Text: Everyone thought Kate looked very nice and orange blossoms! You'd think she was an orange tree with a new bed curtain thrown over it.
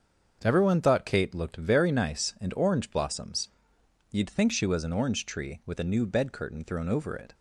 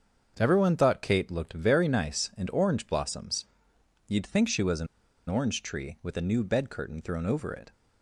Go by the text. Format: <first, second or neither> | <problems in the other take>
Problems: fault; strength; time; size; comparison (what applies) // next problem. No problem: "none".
first | starts louder than the rest; until 1.3 s; 7 dB; also in the first // pauses between "an" and "orange"; at 4.8 s; 0.42 s long